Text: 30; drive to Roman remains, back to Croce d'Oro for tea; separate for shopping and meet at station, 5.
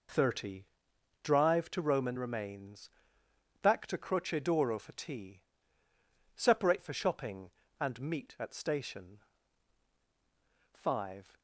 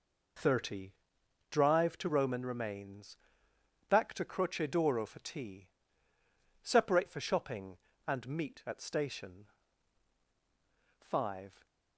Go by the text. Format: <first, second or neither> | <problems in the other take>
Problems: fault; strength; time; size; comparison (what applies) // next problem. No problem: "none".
neither | none